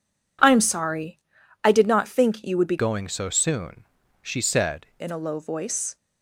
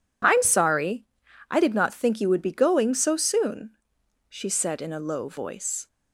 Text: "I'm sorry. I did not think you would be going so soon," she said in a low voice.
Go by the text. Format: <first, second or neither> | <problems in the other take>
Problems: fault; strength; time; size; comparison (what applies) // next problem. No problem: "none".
second | changes voice from "going" to "said"; from 2.7 to 4.8 s; 2.1 s long